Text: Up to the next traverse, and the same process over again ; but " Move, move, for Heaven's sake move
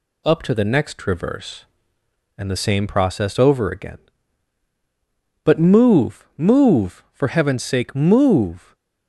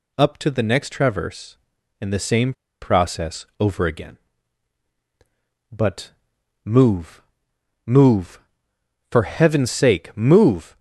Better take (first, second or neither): first